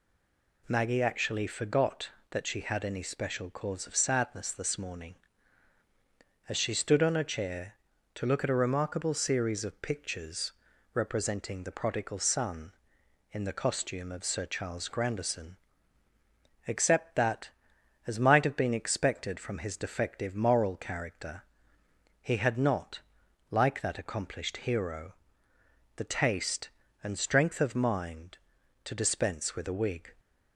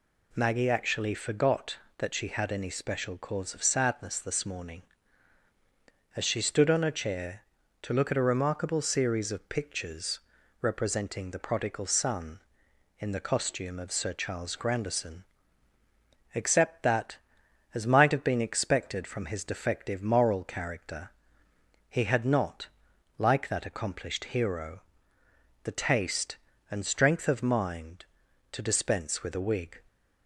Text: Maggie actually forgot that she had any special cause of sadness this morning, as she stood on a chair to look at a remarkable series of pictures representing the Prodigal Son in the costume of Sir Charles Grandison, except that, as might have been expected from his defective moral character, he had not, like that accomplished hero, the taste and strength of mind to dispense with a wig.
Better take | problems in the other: second | stays silent before the first word; slight; until 0.6 s; 0.6 s long // pauses between "pictures" and "representing"; at 10.5 s; 0.42 s long; also in the second

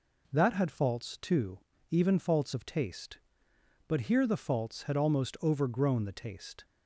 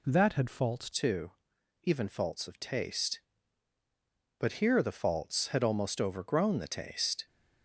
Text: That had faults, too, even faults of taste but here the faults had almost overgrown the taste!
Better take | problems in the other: first | changes voice at "too"; from 0.9 s on; 6.3 s long

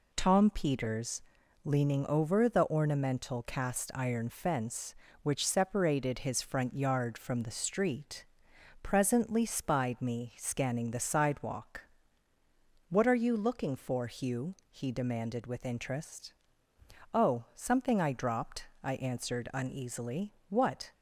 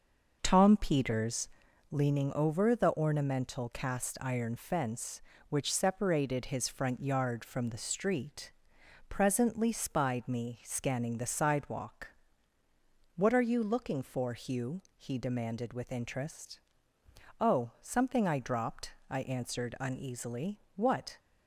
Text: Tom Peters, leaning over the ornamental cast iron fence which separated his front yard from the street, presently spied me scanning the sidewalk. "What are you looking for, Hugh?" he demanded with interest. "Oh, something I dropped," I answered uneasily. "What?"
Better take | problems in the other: first | starts louder than the rest; noticeable; until 1.9 s; 6 dB

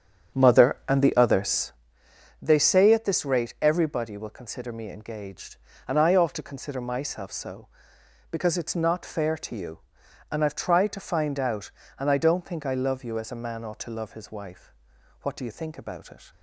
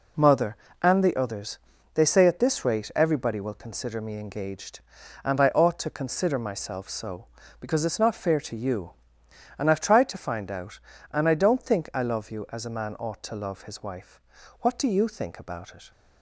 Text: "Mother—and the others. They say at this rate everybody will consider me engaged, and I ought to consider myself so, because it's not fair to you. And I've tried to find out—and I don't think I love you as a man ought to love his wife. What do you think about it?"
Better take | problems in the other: second | starts louder than the rest; strong; until 1.9 s; 8 dB

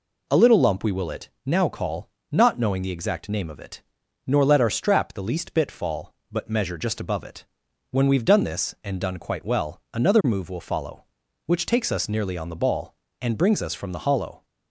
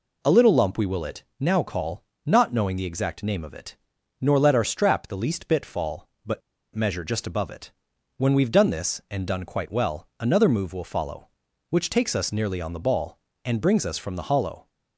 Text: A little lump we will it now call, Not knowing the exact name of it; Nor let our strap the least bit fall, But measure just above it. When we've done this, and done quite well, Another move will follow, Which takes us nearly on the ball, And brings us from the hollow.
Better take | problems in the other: first | pauses between "it" and "now"; slight; at 1.2 s; 0.16 s long; slight in the first // pauses between "But" and "measure"; slight; at 6.4 s; 0.35 s long

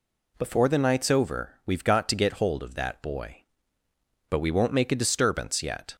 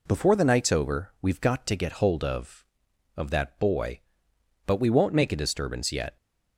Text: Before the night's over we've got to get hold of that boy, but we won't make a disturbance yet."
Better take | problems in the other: first | says "of" twice; at 3.1 s

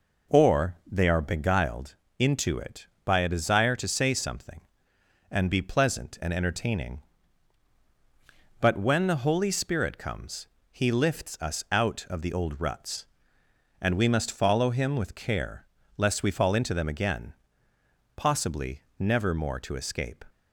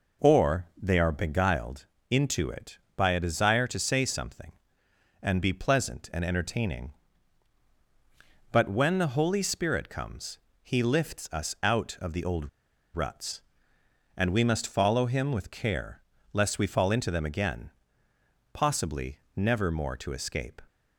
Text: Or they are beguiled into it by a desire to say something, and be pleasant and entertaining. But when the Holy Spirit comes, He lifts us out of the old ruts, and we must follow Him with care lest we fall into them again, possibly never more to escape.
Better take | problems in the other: first | pauses between "beguiled" and "into"; slight; at 1.8 s; 0.24 s long; slight in the first // pauses between "old" and "ruts"; noticeable; at 12.4 s; 0.46 s long // pauses between "care" and "lest"; slight; at 16.0 s; 0.32 s long; slight in the first // pauses between "possibly" and "never"; slight; at 19.1 s; 0.18 s long; slight in the first

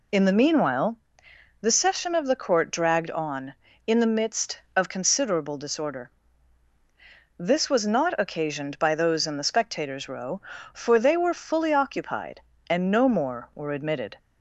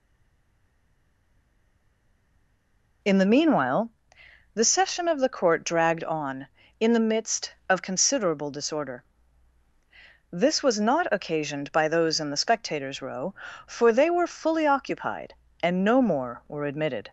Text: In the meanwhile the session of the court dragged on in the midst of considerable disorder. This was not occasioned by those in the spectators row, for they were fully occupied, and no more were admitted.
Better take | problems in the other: first | stays silent before the first word; strong; until 3.0 s; 3.0 s long // pauses between "meanwhile" and "the"; noticeable; at 3.8 s; 0.64 s long; noticeable in the first

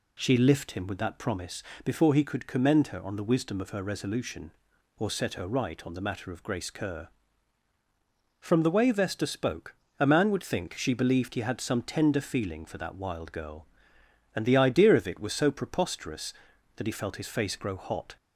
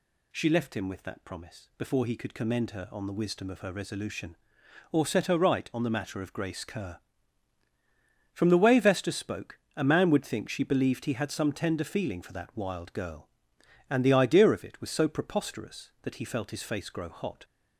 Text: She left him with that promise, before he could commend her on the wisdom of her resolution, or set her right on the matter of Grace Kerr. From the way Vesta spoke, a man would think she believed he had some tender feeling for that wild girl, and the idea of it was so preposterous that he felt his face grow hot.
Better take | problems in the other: second | says "lift" for "left"; at 0.3 s

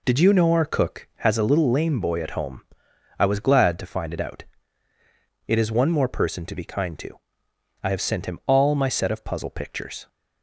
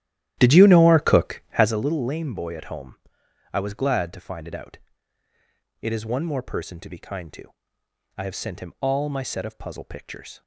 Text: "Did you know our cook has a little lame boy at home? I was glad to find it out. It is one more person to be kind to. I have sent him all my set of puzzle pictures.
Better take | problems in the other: first | starts louder than the rest; strong; until 1.8 s; 13 dB

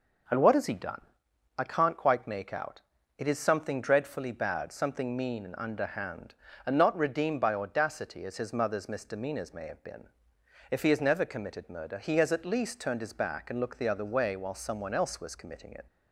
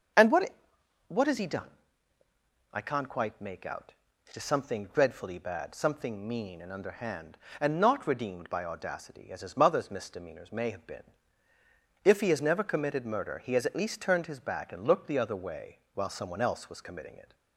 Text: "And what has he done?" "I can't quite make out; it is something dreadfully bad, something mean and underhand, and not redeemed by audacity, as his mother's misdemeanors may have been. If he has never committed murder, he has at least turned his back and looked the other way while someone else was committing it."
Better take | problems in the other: first | starts louder than the rest; until 1.7 s; 7 dB // says "what" twice; at 1.0 s

